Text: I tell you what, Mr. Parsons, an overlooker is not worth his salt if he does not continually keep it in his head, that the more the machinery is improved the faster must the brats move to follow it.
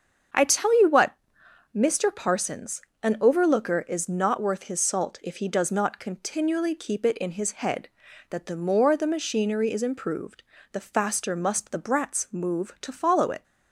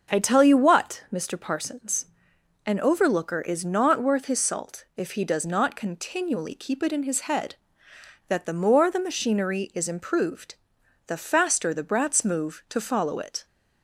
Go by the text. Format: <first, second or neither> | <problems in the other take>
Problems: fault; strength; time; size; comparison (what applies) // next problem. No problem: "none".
first | starts louder than the rest; noticeable; until 1.1 s; 6 dB; also in the first // pauses between "improved" and "the"; noticeable; at 10.5 s; 0.52 s long; slight in the first // skips "must"; at 11.7 s